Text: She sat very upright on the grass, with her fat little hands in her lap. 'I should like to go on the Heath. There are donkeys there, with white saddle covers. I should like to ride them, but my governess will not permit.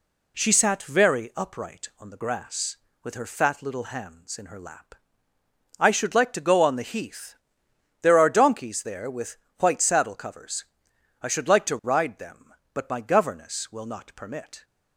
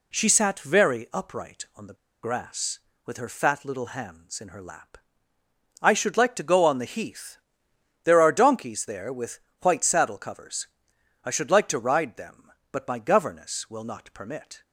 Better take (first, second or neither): first